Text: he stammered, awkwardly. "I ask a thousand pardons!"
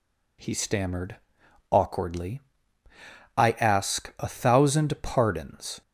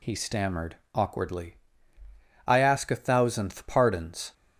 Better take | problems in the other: first | says "thousandth" for "thousand"; at 2.9 s

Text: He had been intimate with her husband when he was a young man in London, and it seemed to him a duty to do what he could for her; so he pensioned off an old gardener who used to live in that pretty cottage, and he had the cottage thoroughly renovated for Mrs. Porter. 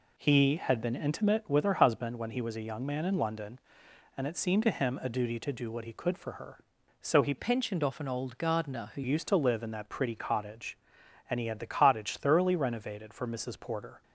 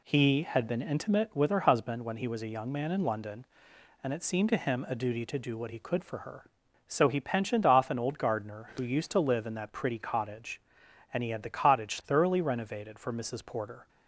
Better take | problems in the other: second | changes voice from "pensioned" to "who"; from 7.3 to 9.0 s; 1.7 s long

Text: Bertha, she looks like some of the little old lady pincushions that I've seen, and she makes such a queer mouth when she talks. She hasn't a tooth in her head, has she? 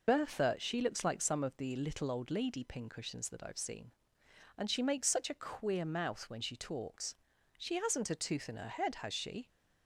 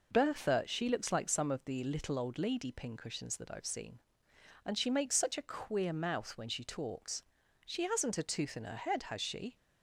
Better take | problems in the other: second | loses the start of "Bertha"; at 0.0 s; 50 ms

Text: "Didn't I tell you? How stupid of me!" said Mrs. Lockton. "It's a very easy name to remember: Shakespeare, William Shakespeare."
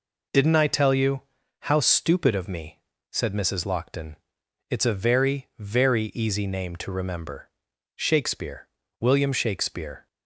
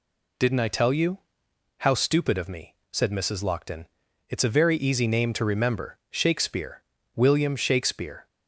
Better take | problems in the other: second | says "very" twice; at 5.5 s

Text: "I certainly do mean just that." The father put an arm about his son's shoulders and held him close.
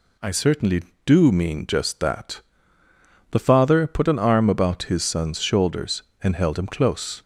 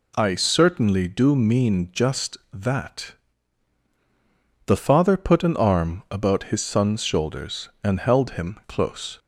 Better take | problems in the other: neither | none

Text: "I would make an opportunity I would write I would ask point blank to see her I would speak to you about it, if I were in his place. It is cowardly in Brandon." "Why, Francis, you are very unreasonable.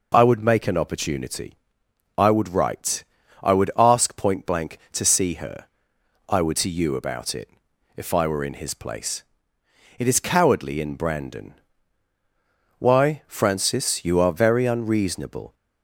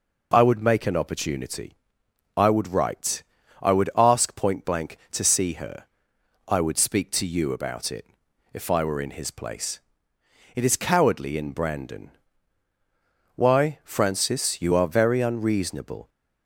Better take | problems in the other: second | pauses between "opportunity" and "I"; noticeable; at 1.5 s; 0.62 s long; noticeable in the second // pauses between "write" and "I"; at 3.0 s; 0.38 s long; also in the second // pauses between "her" and "I"; noticeable; at 5.6 s; 0.64 s long; noticeable in the second // skips "speak"; at 6.5 s

